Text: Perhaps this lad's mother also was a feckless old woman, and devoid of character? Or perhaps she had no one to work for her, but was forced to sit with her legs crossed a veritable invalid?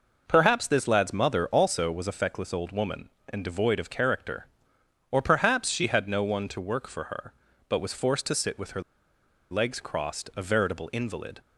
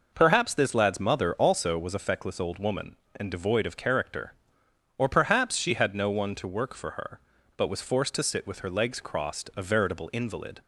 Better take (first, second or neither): second